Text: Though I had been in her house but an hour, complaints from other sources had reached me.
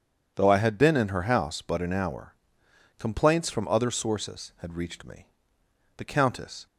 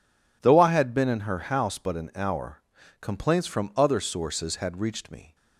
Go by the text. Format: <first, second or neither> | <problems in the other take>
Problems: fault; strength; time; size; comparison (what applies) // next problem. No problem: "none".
second | goes on to say "The Countess"; noticeable; from 5.9 s on; 0.68 s long